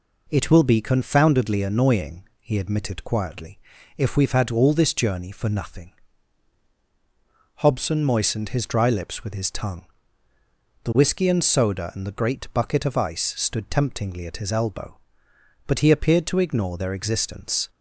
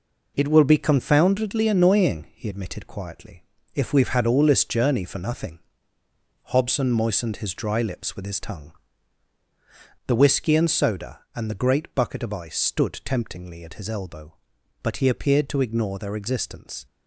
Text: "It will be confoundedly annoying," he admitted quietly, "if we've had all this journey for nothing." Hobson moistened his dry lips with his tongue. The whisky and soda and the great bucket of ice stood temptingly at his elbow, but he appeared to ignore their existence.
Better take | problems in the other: neither | none

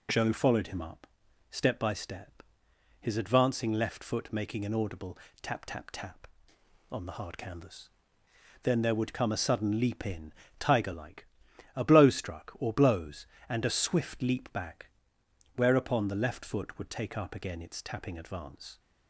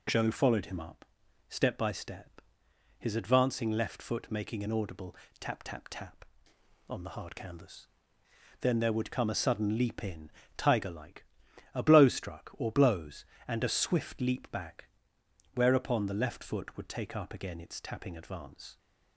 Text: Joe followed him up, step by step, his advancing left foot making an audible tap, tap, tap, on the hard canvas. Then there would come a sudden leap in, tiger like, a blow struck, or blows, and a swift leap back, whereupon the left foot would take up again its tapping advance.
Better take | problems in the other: neither | pauses between "audible" and "tap"; slight; the same in both

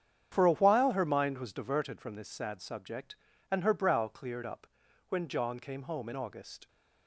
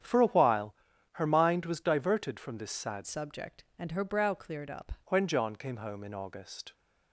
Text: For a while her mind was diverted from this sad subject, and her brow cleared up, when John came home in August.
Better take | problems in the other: first | starts louder than the rest; strong; until 1.4 s; 9 dB; strong in the first // pauses between "while" and "her"; at 0.7 s; 0.38 s long // changes voice from "subject" to "up"; from 3.0 to 4.9 s; 1.9 s long

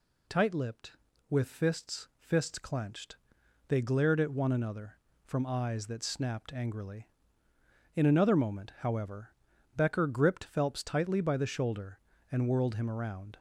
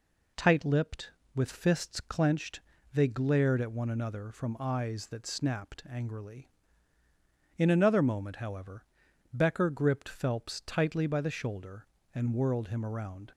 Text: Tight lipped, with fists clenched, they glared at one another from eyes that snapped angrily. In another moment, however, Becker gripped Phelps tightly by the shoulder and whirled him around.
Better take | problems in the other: second | says "fists" twice; at 2.1 s

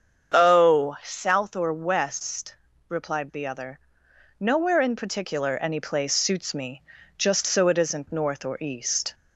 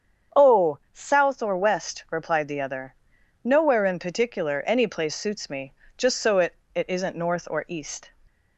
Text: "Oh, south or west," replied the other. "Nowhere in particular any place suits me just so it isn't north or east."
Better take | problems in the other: first | starts louder than the rest; strong; until 1.5 s; 7.5 dB; strong in the first // pauses between "me" and "just"; slight; at 5.7 s; 0.24 s long; slight in the first // says "it" twice; at 6.7 s

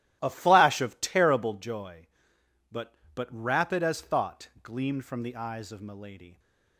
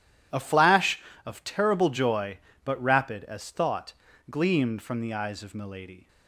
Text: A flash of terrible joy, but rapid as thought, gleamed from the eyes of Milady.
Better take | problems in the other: second | starts louder than the rest; strong; until 1.2 s; 13 dB // says "but" twice; at 3.1 s

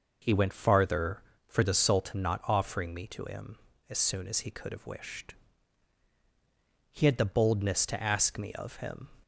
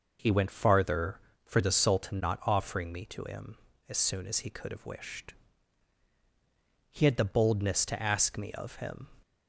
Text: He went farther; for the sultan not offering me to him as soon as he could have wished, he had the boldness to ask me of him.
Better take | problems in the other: neither | none

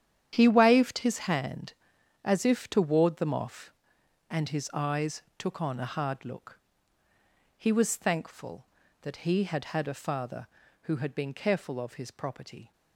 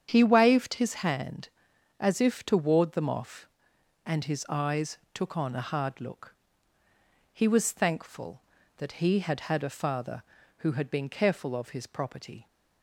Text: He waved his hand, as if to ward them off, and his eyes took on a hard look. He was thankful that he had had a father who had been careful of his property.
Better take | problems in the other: second | gets quieter; strong; throughout; 12.5 dB // starts louder than the rest; strong; until 1.3 s; 10 dB; strong in the second // pauses between "eyes" and "took"; slight; at 5.2 s; 0.16 s long; slight in the second

